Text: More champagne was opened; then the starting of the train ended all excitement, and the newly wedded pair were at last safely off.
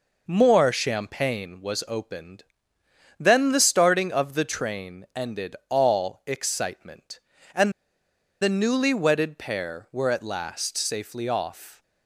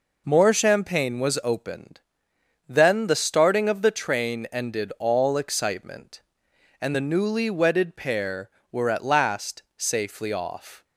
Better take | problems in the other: second | pauses between "and" and "the"; noticeable; at 7.7 s; 0.70 s long

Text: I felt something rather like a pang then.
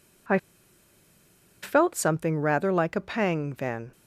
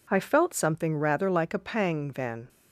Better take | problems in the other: second | pauses between "I" and "felt"; at 0.3 s; 1.2 s long

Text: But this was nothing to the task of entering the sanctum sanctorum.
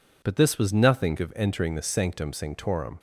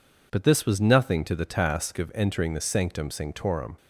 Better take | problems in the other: second | skips "to the task"; at 1.1 s

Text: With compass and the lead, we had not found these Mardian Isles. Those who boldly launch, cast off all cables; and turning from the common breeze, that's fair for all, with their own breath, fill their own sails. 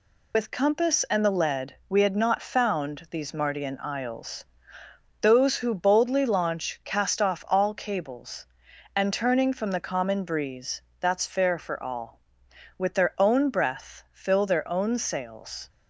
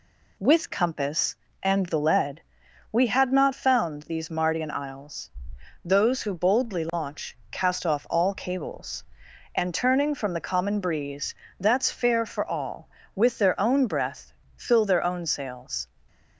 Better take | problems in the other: second | loses the start of "With"; at 0.3 s; 100 ms

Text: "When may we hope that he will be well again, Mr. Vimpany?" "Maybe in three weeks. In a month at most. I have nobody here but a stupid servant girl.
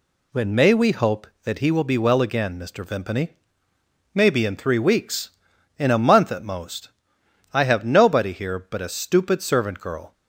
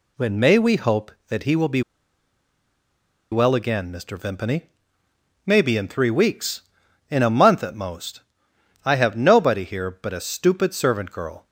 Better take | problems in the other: first | pauses between "be" and "well"; strong; at 1.8 s; 1.5 s long

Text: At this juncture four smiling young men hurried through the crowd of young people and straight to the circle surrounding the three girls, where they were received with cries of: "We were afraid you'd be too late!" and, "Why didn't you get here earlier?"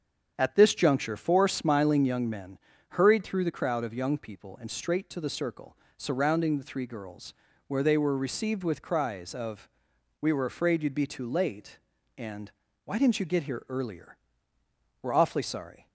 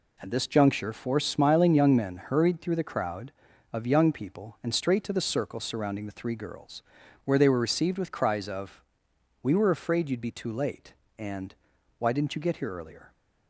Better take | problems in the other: second | starts louder than the rest; strong; until 1.3 s; 7.5 dB // pauses between "men" and "hurried"; slight; at 2.5 s; 0.32 s long // pauses between "circle" and "surrounding"; slight; at 5.7 s; 0.20 s long // goes on to say "We're awfully sorry"; noticeable; from 15.0 s on; 0.86 s long

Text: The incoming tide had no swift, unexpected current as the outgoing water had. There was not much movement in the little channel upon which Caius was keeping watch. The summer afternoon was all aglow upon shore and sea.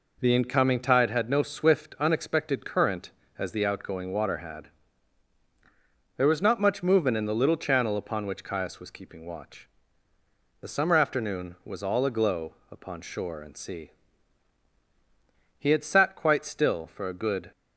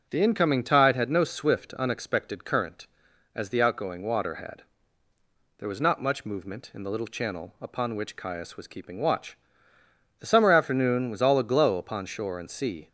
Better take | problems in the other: second | goes on to say "He had sat quite still for a good"; strong; from 15.5 s on; 1.9 s long

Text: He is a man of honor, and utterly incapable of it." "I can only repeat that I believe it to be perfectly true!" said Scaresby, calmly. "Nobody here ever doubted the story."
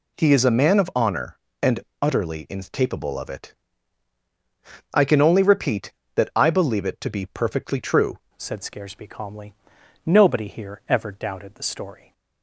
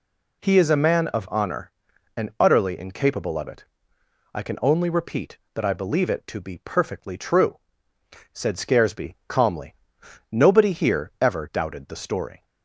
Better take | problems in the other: second | pauses between "and" and "utterly"; slight; at 1.8 s; 0.20 s long // changes voice at "said"; from 8.3 s on; 3.8 s long

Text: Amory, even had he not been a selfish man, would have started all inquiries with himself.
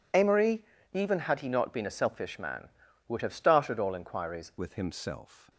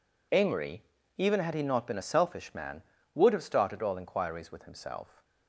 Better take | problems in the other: second | changes voice at "with"; from 4.5 s on; 0.9 s long

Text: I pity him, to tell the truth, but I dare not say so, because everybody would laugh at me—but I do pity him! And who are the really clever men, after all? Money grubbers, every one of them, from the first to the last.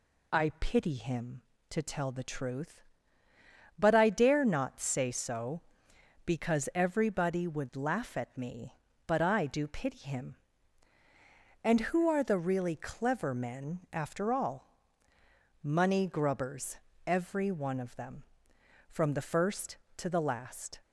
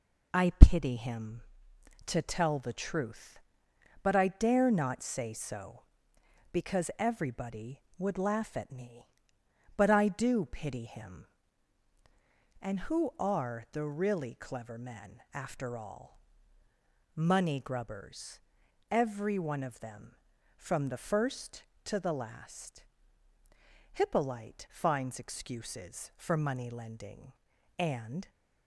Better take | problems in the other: first | goes on to say "Hippolyte finds excuses for money lending and"; strong; from 23.9 s on; 4.3 s long

